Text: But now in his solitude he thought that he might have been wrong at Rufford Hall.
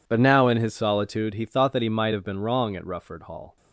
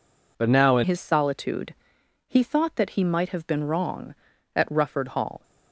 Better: first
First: none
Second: changes voice at "his"; from 0.8 s on; 4.6 s long // pauses between "solitude" and "he"; noticeable; at 1.7 s; 0.54 s long

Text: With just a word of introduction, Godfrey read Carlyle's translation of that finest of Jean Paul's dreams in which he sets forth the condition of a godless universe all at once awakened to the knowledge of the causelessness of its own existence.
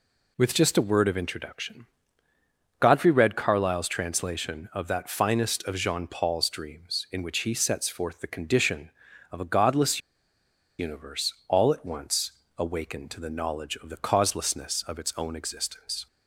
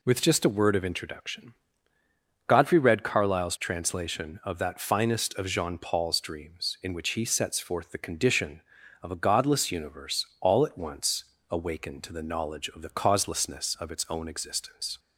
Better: second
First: pauses between "godless" and "universe"; noticeable; at 9.9 s; 0.78 s long // pauses between "once" and "awakened"; slight; at 12.3 s; 0.24 s long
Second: pauses between "once" and "awakened"; slight; at 11.2 s; 0.24 s long

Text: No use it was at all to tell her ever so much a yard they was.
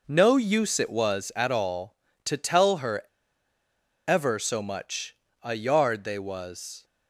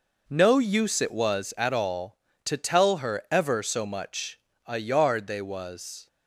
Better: second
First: pauses between "her" and "ever"; at 3.0 s; 1.0 s long // pauses between "much" and "a"; slight; at 5.1 s; 0.28 s long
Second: pauses between "much" and "a"; slight; at 4.3 s; 0.28 s long

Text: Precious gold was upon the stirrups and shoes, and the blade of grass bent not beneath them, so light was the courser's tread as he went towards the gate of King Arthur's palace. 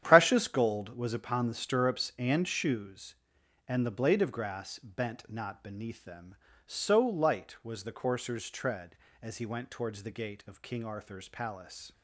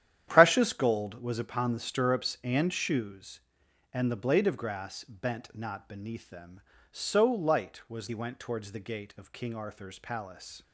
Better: first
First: starts louder than the rest; strong; until 1.0 s; 10 dB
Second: starts louder than the rest; strong; until 1.2 s; 10.5 dB // skips "the courser's tread as"; at 8.0 s

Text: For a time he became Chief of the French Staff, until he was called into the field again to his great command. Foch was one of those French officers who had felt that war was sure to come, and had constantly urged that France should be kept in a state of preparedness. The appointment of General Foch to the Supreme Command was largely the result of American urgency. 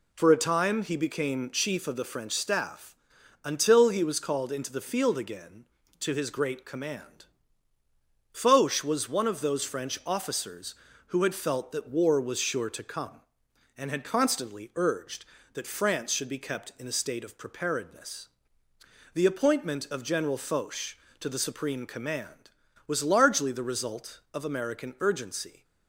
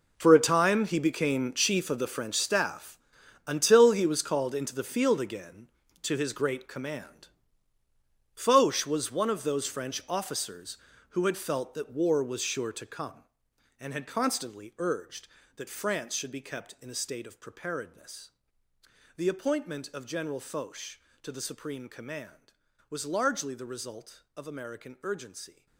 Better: first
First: none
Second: gets quieter; strong; throughout; 14 dB

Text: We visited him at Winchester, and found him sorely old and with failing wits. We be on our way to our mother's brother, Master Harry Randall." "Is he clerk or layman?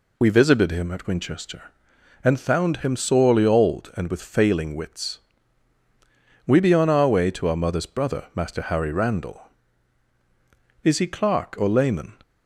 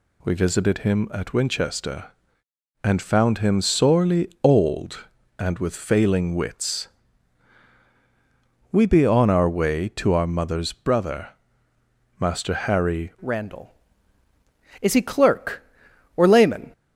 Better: first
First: none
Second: changes voice at "Randall"; from 13.2 s on; 3.5 s long

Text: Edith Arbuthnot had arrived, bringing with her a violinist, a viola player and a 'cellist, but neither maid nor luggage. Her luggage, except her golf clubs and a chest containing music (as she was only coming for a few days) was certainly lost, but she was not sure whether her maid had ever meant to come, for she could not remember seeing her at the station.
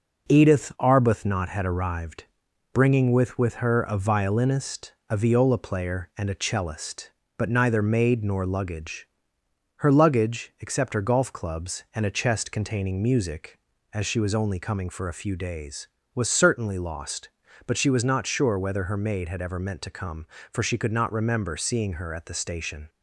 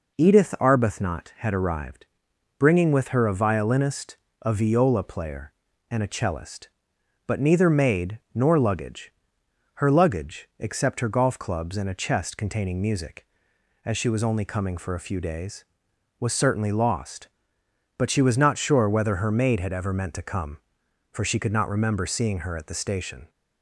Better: second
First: says "with" twice; at 3.3 s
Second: none

